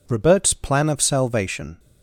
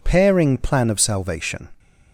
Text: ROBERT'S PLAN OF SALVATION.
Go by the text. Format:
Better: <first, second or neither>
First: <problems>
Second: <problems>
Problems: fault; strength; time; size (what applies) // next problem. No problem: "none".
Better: first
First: none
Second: says "Pairing" for "ROBERT'S"; at 0.0 s